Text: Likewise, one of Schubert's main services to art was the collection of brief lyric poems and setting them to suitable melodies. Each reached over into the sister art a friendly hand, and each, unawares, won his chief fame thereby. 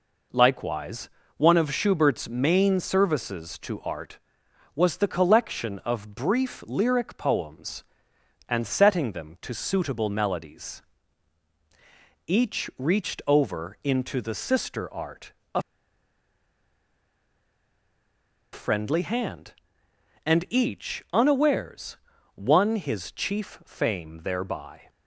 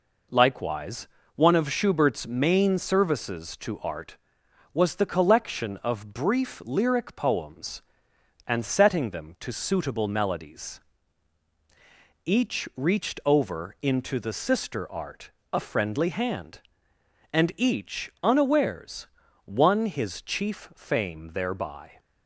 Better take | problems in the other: second | pauses between "art" and "a"; slight; at 15.3 s; 0.22 s long; slight in the second // pauses between "a" and "friendly"; strong; at 15.6 s; 2.9 s long

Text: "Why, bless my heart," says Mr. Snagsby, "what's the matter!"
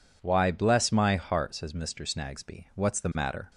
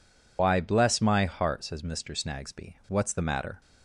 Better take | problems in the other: first | loses the start of "Why"; at 0.3 s; 85 ms

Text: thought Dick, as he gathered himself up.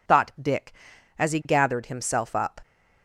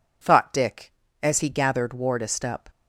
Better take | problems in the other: first | says "wardest" for "himself"; at 1.9 s

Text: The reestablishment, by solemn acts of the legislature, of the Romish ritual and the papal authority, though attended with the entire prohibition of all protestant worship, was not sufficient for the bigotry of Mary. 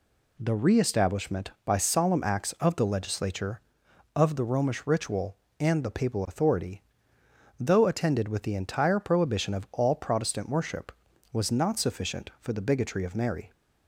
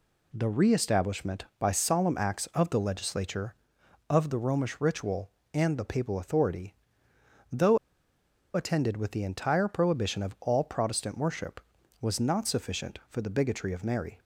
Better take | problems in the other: first | pauses between "though" and "attended"; noticeable; at 7.7 s; 0.77 s long

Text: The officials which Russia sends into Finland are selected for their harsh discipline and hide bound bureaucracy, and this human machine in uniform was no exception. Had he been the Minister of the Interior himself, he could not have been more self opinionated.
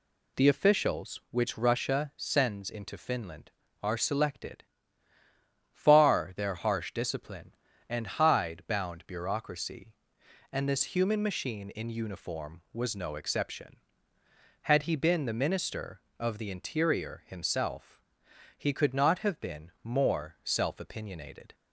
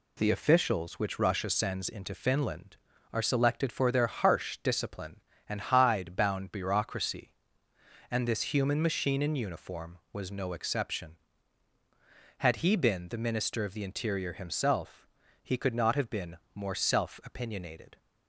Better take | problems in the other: second | says "far" for "for"; at 5.7 s

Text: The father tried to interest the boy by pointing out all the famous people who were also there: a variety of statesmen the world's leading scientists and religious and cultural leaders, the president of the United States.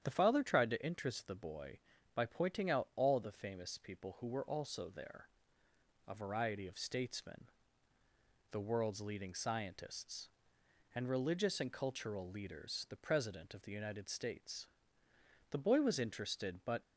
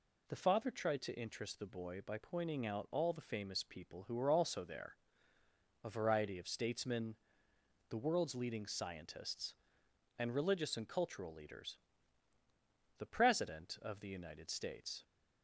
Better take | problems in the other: second | starts louder than the rest; strong; until 1.0 s; 9.5 dB // pauses between "statesmen" and "the"; at 7.4 s; 1.0 s long; noticeable in the second // goes on to say "The boy was interested but"; noticeable; from 15.5 s on; 1.3 s long

